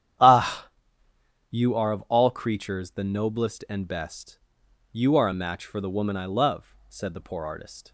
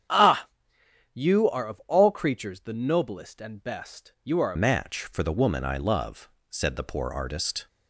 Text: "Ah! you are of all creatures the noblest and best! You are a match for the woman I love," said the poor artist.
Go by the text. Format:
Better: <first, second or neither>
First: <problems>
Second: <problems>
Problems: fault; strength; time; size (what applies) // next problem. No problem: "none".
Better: first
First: starts louder than the rest; strong; until 2.0 s; 10 dB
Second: starts louder than the rest; strong; until 1.7 s; 8.5 dB // changes voice at "match"; from 4.5 s on; 3.1 s long